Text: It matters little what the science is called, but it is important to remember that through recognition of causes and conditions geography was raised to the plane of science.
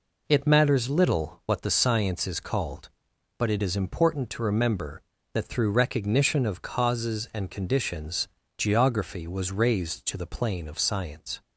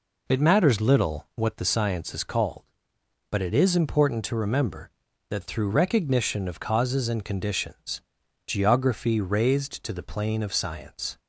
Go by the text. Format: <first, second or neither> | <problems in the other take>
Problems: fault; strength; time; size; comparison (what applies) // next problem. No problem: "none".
first | pauses between "conditions" and "geography"; noticeable; at 8.0 s; 0.46 s long; slight in the first // skips "was"; at 9.2 s